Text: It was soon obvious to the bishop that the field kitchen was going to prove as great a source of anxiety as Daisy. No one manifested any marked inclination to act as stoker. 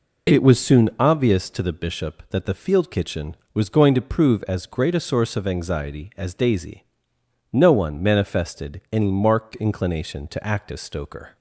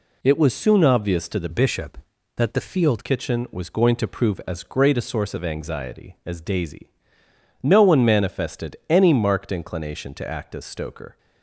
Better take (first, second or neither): first